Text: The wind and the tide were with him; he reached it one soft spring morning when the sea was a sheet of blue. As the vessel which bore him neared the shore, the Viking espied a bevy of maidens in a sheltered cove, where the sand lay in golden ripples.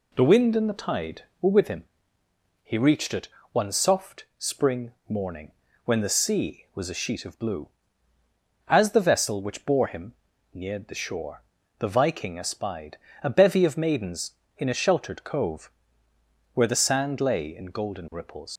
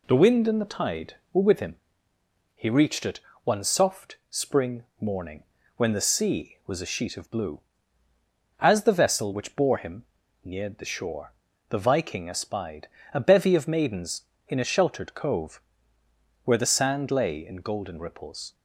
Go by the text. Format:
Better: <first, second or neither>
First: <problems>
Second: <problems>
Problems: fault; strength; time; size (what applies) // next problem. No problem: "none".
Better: second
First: pauses between "it" and "one"; slight; at 3.2 s; 0.24 s long // pauses between "spring" and "morning"; slight; at 4.9 s; 0.16 s long // pauses between "morning" and "when"; slight; at 5.5 s; 0.34 s long // pauses between "him" and "neared"; at 10.1 s; 0.40 s long // pauses between "espied" and "a"; slight; at 12.9 s; 0.24 s long // leaves "ripples" unfinished; at 18.5 s; 120 ms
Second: pauses between "it" and "one"; slight; at 3.1 s; 0.24 s long // pauses between "spring" and "morning"; slight; at 4.8 s; 0.16 s long // pauses between "morning" and "when"; slight; at 5.4 s; 0.34 s long // pauses between "him" and "neared"; at 10.0 s; 0.40 s long // pauses between "espied" and "a"; slight; at 12.8 s; 0.24 s long